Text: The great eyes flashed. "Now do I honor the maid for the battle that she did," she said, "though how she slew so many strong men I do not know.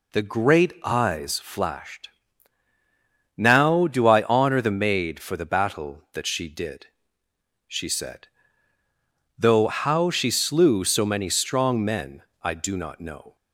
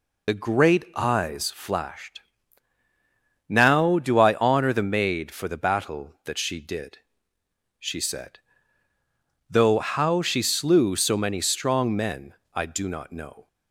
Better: first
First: pauses between "men" and "I"; slight; at 12.2 s; 0.20 s long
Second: loses the start of "The"; at 0.2 s; 30 ms // pauses between "men" and "I"; slight; at 12.3 s; 0.20 s long

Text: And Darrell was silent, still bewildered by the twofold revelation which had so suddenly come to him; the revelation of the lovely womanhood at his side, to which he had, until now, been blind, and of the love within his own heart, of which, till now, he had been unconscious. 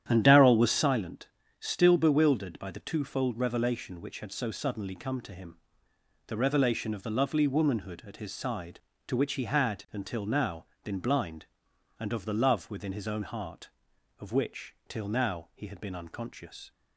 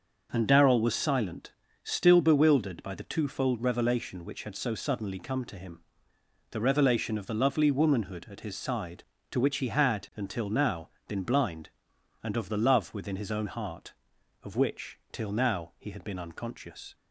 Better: second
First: starts louder than the rest; strong; until 1.0 s; 10 dB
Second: none

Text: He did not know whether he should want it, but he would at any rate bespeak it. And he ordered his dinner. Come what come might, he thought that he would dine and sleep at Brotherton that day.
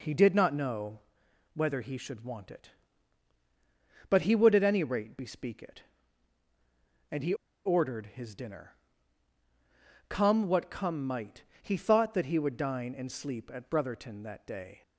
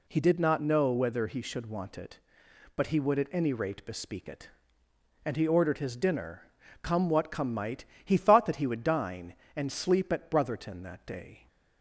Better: second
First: pauses between "know" and "whether"; noticeable; at 0.9 s; 0.56 s long // pauses between "he" and "ordered"; slight; at 7.3 s; 0.30 s long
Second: none

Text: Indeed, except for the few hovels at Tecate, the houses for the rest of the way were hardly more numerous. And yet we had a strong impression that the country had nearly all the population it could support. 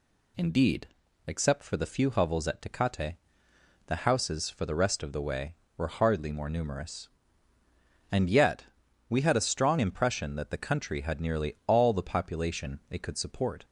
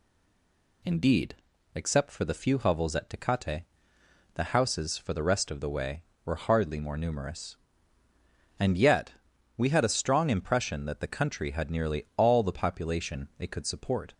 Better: first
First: pauses between "yet" and "we"; at 8.6 s; 0.44 s long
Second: stays silent before the first word; slight; until 0.8 s; 0.8 s long // pauses between "yet" and "we"; at 9.1 s; 0.44 s long

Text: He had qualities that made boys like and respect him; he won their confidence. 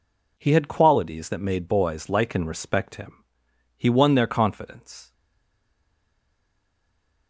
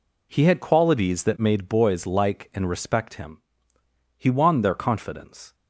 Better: second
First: stays silent after the last word; from 5.1 s on; 2.1 s long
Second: none

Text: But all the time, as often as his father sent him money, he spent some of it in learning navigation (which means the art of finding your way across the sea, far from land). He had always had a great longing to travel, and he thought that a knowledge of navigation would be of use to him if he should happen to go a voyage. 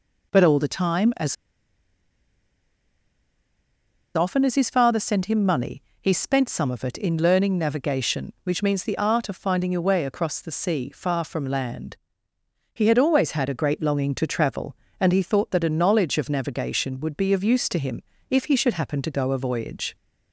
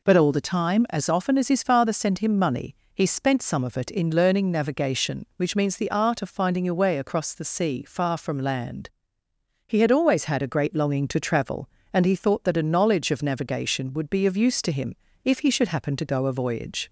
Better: second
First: pauses between "as" and "often"; strong; at 1.3 s; 2.8 s long // pauses between "him" and "if"; slight; at 18.0 s; 0.26 s long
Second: pauses between "him" and "if"; slight; at 14.9 s; 0.27 s long

